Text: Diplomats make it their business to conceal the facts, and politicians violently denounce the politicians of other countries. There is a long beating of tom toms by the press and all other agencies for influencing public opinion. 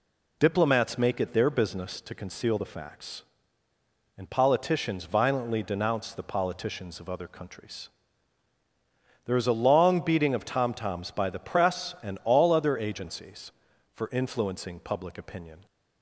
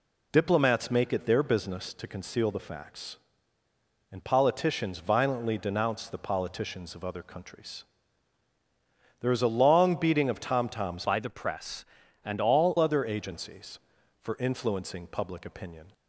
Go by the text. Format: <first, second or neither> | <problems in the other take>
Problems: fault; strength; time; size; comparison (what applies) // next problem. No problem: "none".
first | changes voice from "by" to "all"; from 11.0 to 12.7 s; 1.7 s long